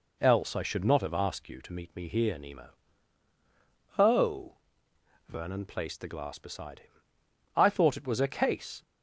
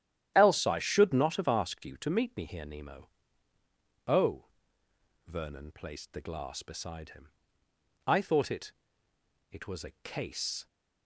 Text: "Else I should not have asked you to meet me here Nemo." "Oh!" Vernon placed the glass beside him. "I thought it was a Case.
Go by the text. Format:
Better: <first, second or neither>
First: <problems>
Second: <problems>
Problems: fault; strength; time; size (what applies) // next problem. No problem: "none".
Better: first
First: none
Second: starts louder than the rest; strong; until 1.3 s; 11 dB // says "it" twice; at 9.5 s